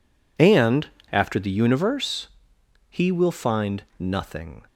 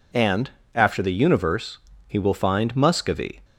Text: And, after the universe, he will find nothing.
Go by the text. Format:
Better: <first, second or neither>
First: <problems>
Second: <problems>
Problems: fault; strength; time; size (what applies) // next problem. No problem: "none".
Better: first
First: none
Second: says "muscovy" for "nothing"; at 2.7 s